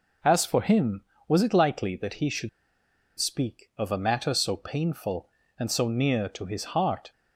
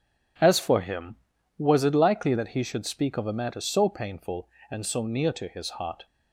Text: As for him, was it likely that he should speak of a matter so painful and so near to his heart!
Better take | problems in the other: second | pauses between "should" and "speak"; noticeable; at 2.4 s; 0.69 s long

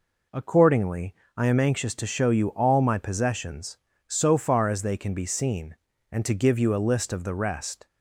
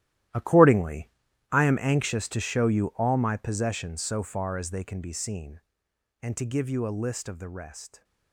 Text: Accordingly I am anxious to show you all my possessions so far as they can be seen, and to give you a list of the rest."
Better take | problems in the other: first | gets quieter; strong; throughout; 14.5 dB // pauses between "Accordingly" and "I"; at 1.0 s; 0.42 s long; slight in the first

